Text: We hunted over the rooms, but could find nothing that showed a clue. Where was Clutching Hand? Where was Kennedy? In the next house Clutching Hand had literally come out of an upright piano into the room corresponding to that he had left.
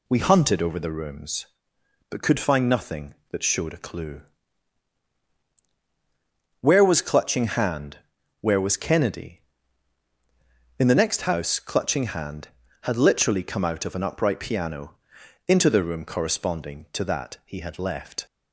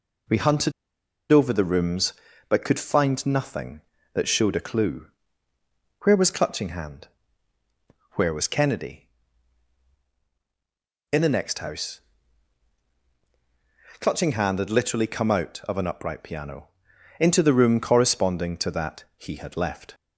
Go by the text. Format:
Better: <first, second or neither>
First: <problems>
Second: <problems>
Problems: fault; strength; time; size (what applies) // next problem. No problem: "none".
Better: first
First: pauses between "piano" and "into"; noticeable; at 14.9 s; 0.54 s long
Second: pauses between "hunted" and "over"; noticeable; at 0.7 s; 0.60 s long // pauses between "house" and "Clutching"; strong; at 12.0 s; 2.0 s long // pauses between "piano" and "into"; noticeable; at 16.6 s; 0.52 s long